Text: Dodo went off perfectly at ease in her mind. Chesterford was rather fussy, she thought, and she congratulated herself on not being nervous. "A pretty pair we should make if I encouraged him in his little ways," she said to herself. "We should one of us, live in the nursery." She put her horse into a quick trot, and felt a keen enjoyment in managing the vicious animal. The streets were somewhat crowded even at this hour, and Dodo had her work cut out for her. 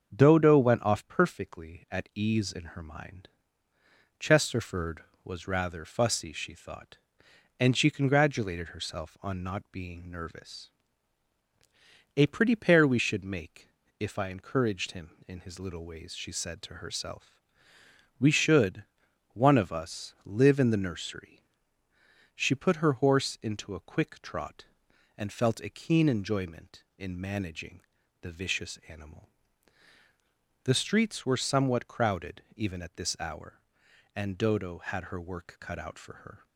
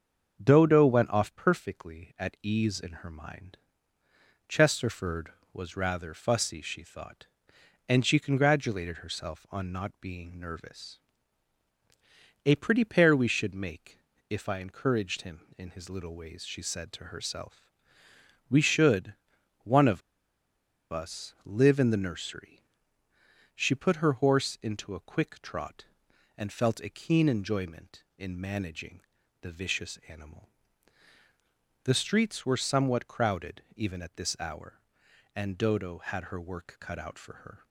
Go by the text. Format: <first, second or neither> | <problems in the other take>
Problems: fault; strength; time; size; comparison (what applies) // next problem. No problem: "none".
first | starts louder than the rest; until 1.4 s; 6.5 dB; also in the first // pauses between "make" and "if"; slight; at 13.9 s; 0.32 s long; slight in the first // pauses between "should" and "one"; noticeable; at 19.1 s; 0.48 s long; noticeable in the first // pauses between "of" and "us"; noticeable; at 20.0 s; 0.90 s long // pauses between "managing" and "the"; at 29.0 s; 0.38 s long; also in the first